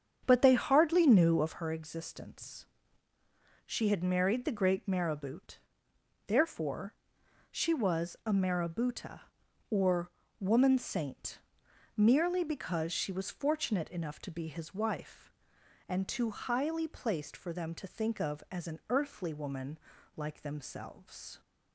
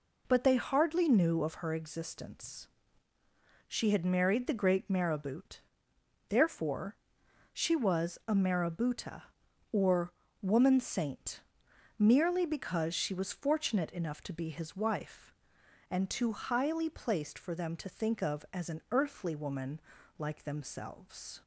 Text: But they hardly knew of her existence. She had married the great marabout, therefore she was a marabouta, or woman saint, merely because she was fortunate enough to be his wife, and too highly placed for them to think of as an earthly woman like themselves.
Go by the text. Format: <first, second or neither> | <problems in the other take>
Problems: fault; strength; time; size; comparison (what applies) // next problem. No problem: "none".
second | starts louder than the rest; strong; until 1.7 s; 7.5 dB // pauses between "therefore" and "she"; noticeable; at 6.9 s; 0.56 s long; noticeable in the second // pauses between "or" and "woman"; slight; at 10.1 s; 0.30 s long; slight in the second // pauses between "woman" and "like"; at 19.7 s; 0.38 s long; also in the second